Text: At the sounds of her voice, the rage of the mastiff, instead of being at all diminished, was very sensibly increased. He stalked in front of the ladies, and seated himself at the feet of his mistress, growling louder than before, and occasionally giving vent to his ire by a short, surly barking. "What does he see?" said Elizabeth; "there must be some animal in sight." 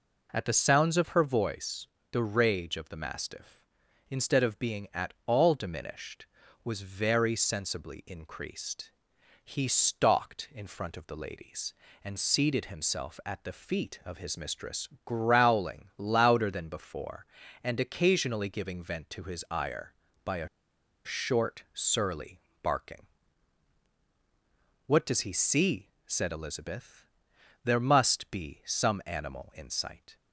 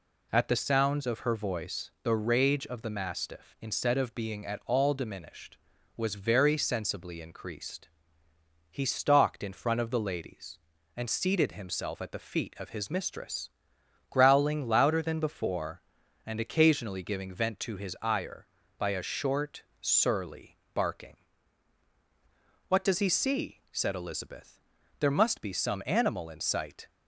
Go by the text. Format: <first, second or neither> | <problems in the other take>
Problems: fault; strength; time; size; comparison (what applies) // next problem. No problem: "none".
second | pauses between "a" and "short"; noticeable; at 20.4 s; 0.57 s long // pauses between "surly" and "barking"; slight; at 22.3 s; 0.22 s long; slight in the second